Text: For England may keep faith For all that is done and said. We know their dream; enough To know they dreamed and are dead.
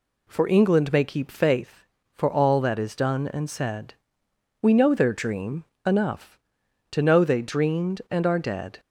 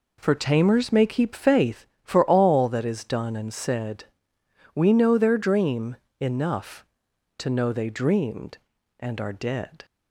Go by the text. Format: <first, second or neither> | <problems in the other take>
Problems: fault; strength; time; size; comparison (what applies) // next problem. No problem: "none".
first | says "Tamers" for "England"; at 0.3 s